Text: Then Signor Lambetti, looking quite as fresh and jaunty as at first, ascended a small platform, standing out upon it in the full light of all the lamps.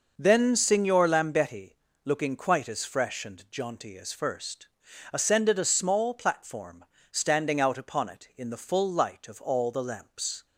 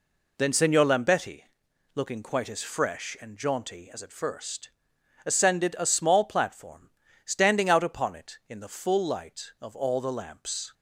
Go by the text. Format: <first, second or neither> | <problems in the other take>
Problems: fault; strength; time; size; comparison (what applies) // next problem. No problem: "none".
second | skips "at"; at 4.1 s